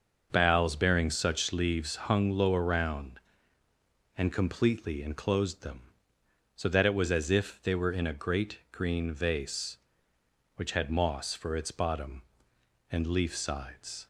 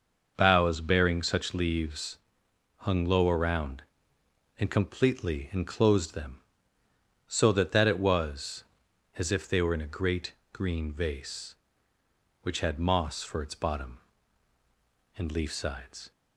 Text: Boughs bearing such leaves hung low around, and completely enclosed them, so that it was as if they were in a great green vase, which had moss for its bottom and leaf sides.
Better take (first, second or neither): first